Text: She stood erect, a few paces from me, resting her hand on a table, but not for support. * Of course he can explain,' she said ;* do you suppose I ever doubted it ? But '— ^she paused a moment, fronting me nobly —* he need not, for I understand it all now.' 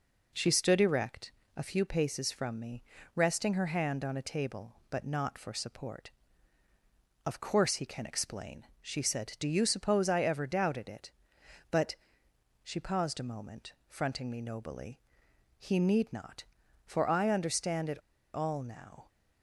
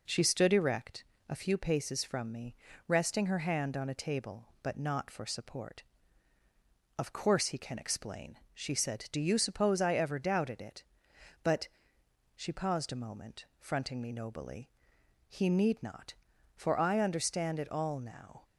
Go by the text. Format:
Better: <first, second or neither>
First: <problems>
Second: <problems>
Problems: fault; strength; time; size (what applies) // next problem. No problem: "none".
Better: second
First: pauses between "it" and "all"; slight; at 18.0 s; 0.34 s long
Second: none